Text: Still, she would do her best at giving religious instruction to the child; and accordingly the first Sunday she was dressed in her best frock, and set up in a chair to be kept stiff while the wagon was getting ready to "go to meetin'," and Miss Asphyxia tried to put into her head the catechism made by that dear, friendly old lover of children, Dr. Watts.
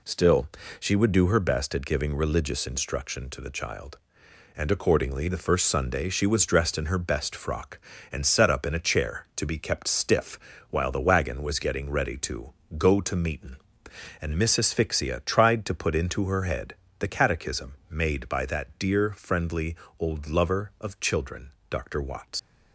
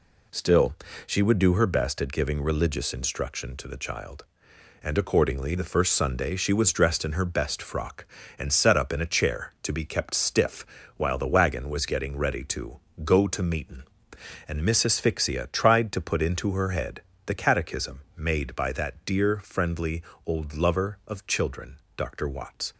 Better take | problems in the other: second | pauses between "stiff" and "while"; slight; at 10.3 s; 0.32 s long; slight in the second // pauses between "to" and "go"; slight; at 12.5 s; 0.24 s long; slight in the second // pauses between "head" and "the"; slight; at 16.7 s; 0.24 s long; slight in the second // pauses between "friendly" and "old"; slight; at 19.7 s; 0.24 s long; slight in the second // leaves "Watts" unfinished; at 22.3 s; 65 ms

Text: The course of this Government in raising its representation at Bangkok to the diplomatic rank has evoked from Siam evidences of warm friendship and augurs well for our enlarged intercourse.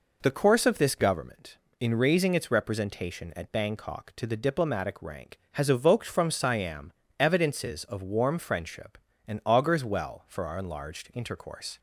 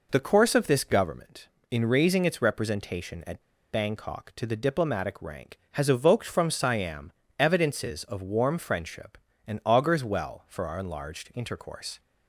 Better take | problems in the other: first | pauses between "at" and "Bangkok"; slight; at 3.4 s; 0.30 s long // pauses between "Siam" and "evidences"; slight; at 7.1 s; 0.26 s long; slight in the first

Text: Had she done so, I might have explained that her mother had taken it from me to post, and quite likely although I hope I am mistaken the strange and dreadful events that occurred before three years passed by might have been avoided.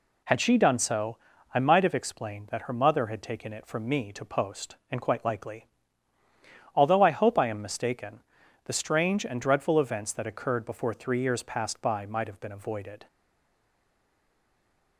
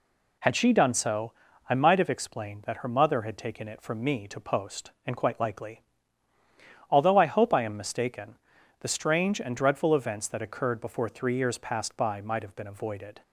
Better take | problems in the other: second | pauses between "likely" and "although"; at 5.6 s; 1.0 s long; also in the second // pauses between "mistaken" and "the"; at 8.2 s; 0.40 s long; also in the second // stays silent after the last word; noticeable; from 13.0 s on; 1.9 s long

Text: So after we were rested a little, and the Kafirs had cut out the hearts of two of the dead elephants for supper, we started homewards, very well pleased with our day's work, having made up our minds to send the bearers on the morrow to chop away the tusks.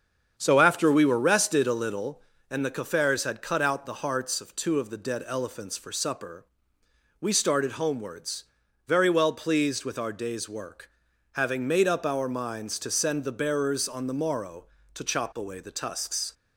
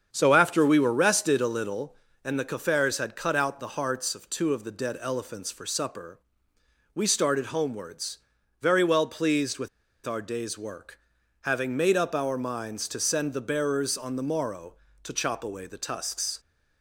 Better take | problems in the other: first | starts louder than the rest; strong; until 1.1 s; 7.5 dB; strong in the first // pauses between "with" and "our"; at 9.6 s; 0.37 s long

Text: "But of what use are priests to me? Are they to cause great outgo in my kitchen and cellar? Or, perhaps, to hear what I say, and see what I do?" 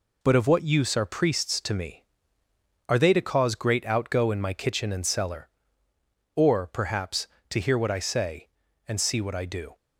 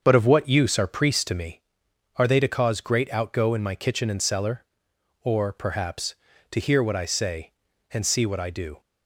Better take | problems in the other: first | starts louder than the rest; until 1.7 s; 7 dB

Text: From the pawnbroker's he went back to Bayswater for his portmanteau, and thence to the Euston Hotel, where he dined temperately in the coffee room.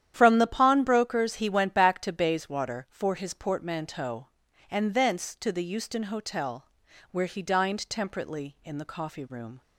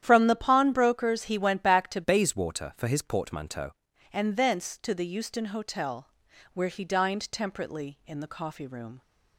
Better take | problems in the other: first | starts louder than the rest; strong; until 1.0 s; 10.5 dB; strong in the first // changes voice from "Bayswater" to "portmanteau"; from 2.0 to 3.7 s; 1.7 s long

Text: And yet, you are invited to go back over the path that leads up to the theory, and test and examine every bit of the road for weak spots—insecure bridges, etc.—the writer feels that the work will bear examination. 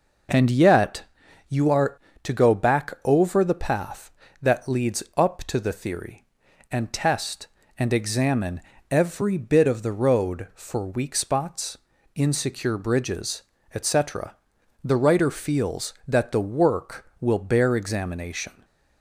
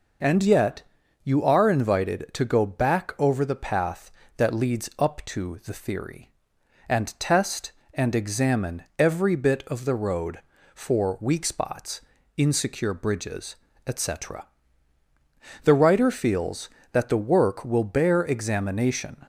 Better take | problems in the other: second | skips "invited"; at 2.0 s // pauses between "examine" and "every"; slight; at 8.6 s; 0.30 s long; slight in the second

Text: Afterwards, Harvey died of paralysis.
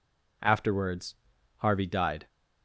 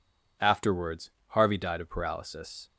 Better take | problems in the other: second | stops before "of paralysis"; at 2.2 s

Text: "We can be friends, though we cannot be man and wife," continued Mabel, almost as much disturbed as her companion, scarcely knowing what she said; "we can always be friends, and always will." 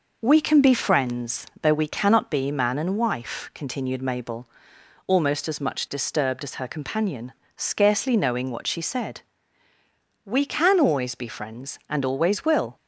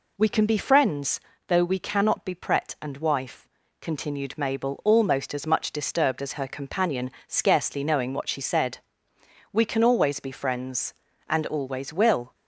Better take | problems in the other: first | says "pret" for "man"; at 2.3 s

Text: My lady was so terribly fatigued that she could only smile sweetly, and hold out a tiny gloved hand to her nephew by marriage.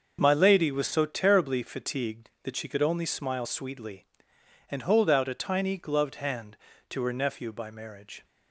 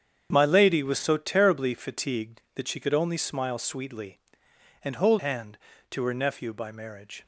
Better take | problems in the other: first | starts louder than the rest; strong; until 1.3 s; 8 dB; also in the first // skips "out a tiny gloved"; at 5.1 s

